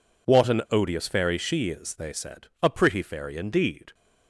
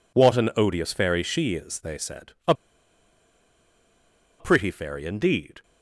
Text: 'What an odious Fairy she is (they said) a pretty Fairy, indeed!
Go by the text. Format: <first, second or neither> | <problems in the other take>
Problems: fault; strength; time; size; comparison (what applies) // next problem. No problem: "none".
first | pauses between "a" and "pretty"; strong; at 2.5 s; 1.8 s long